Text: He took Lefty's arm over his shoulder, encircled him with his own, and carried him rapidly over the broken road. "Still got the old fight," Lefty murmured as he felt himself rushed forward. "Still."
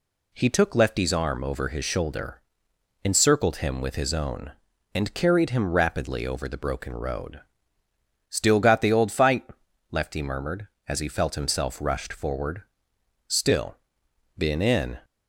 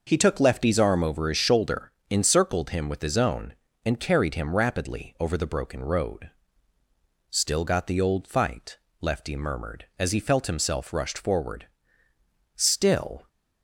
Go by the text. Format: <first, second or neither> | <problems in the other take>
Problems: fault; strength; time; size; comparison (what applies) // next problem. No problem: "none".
second | goes on to say "Been in"; noticeable; from 14.3 s on; 0.62 s long